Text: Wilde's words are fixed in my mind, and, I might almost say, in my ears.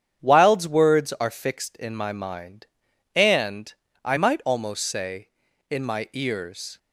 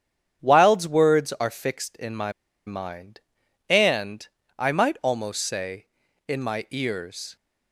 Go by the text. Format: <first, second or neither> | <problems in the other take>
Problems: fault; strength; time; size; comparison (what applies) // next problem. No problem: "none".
first | starts louder than the rest; strong; until 1.4 s; 8.5 dB; strong in the first // pauses between "my" and "mind"; slight; at 2.3 s; 0.35 s long